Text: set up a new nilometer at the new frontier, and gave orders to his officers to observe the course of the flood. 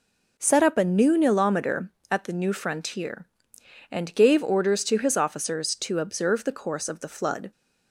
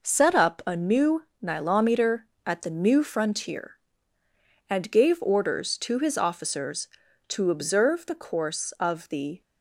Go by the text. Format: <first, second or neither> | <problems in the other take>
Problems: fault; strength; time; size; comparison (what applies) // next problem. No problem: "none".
first | pauses between "new" and "nilometer"; slight; at 1.2 s; 0.18 s long // stops before "flood"; at 9.4 s